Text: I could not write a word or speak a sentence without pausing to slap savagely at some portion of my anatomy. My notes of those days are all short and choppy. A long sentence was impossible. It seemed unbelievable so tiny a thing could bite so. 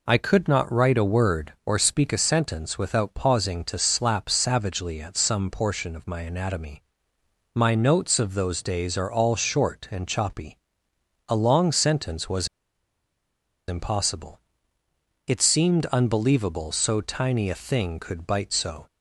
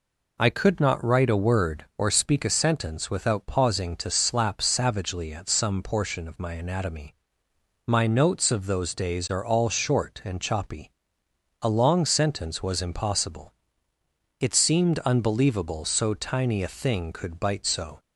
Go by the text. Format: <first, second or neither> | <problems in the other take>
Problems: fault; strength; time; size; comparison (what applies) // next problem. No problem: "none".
second | pauses between "was" and "impossible"; at 12.4 s; 1.2 s long